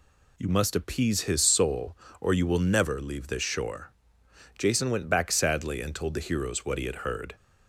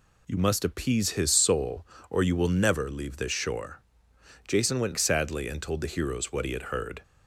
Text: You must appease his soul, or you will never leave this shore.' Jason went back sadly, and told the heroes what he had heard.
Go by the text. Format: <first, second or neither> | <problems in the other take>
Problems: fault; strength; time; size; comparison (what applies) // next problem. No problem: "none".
first | skips "back"; at 4.9 s